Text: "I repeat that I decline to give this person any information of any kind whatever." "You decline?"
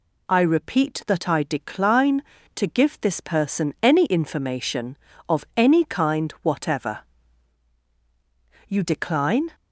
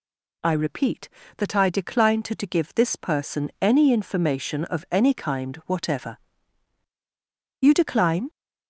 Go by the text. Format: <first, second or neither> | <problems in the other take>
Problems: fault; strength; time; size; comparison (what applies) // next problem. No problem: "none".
first | says "to" twice; at 2.3 s